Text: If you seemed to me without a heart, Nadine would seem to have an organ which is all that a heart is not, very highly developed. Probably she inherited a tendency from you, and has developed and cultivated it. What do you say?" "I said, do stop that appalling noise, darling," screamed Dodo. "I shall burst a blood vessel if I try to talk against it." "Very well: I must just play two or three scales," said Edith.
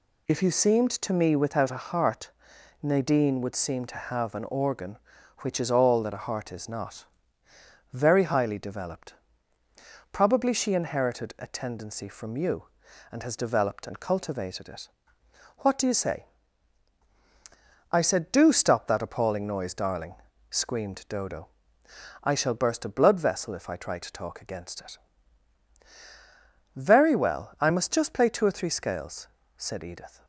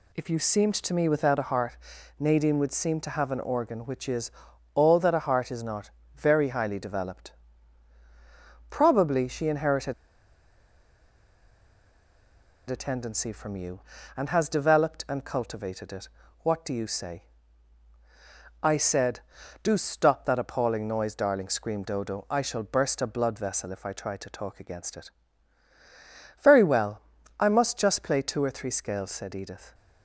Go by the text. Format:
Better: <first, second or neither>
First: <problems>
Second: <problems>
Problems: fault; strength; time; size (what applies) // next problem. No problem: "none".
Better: first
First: none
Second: pauses between "is" and "all"; at 4.3 s; 0.44 s long // pauses between "inherited" and "a"; strong; at 9.9 s; 2.7 s long